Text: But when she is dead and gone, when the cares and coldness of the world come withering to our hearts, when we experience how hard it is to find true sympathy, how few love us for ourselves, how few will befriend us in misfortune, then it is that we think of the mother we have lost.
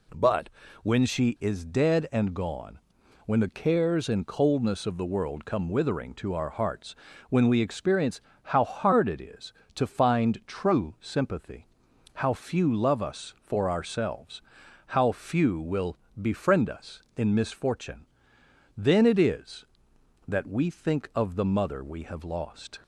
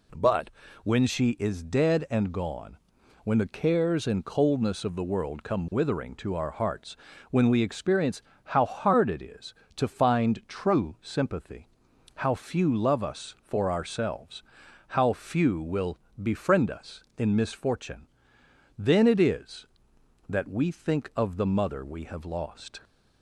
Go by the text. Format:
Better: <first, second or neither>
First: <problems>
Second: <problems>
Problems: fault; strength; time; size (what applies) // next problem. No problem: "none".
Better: neither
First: pauses between "But" and "when"; slight; at 0.4 s; 0.32 s long // pauses between "experience" and "how"; slight; at 8.2 s; 0.24 s long // pauses between "will" and "befriend"; slight; at 15.9 s; 0.24 s long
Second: pauses between "But" and "when"; slight; at 0.5 s; 0.32 s long // pauses between "experience" and "how"; slight; at 8.2 s; 0.24 s long // pauses between "will" and "befriend"; slight; at 15.9 s; 0.24 s long